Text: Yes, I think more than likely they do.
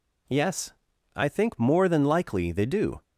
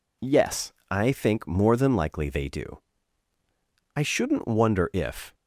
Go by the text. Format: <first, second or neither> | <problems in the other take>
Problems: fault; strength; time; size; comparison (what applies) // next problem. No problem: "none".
first | goes on to say "I shouldn't wonder if"; from 3.9 s on; 1.4 s long